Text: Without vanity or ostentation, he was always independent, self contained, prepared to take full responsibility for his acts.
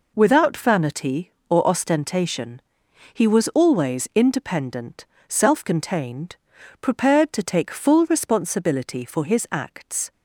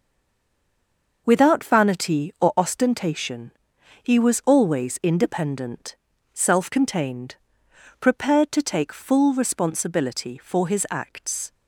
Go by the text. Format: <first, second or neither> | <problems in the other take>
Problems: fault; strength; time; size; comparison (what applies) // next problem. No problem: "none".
first | stays silent before the first word; noticeable; until 1.2 s; 1.2 s long